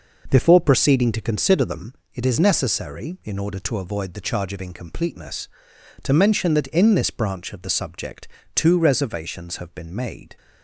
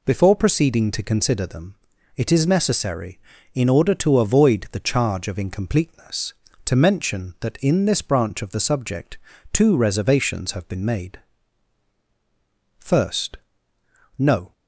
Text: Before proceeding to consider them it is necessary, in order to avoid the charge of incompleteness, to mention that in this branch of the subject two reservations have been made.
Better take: first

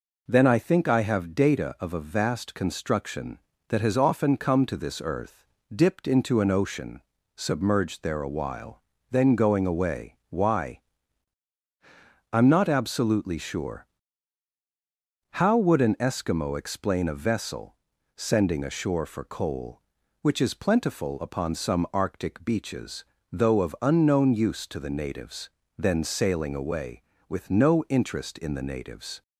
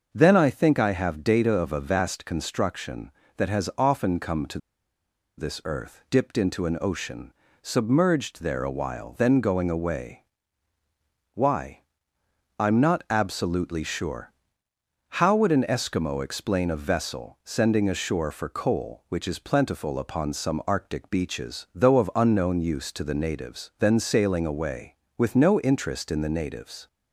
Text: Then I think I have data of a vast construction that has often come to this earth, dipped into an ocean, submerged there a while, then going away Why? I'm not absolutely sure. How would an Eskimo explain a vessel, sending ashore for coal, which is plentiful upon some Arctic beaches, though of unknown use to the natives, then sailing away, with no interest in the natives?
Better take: first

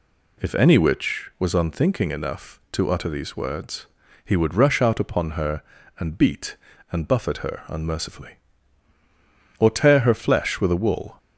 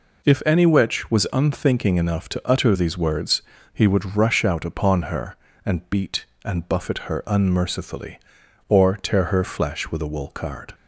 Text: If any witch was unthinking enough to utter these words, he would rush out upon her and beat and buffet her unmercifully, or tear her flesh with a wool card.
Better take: second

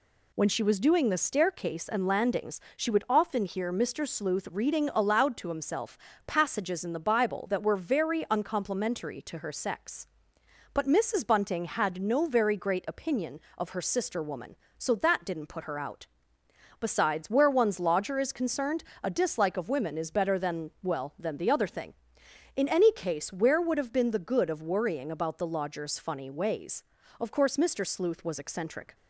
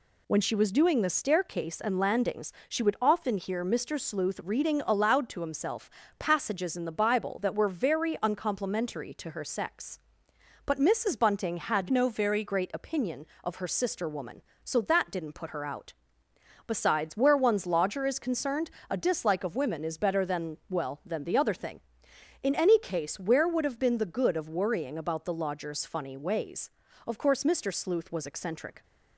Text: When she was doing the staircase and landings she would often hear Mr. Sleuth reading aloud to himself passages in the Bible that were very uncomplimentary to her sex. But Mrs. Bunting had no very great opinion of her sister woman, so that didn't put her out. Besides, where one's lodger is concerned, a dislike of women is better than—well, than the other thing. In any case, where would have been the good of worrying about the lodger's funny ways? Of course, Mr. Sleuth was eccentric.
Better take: first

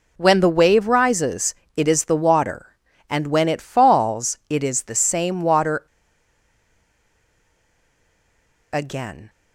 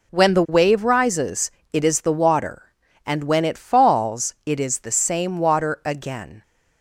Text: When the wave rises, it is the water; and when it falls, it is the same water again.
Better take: second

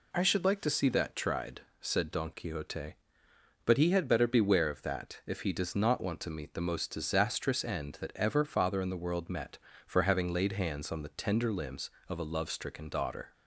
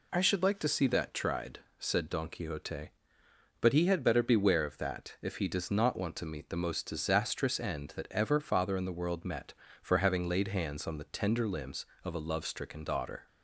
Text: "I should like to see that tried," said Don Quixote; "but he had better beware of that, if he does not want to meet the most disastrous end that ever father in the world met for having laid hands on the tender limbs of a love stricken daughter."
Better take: neither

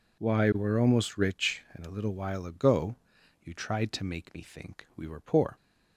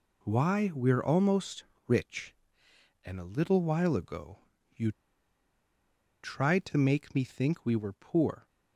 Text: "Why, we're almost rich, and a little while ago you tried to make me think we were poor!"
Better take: first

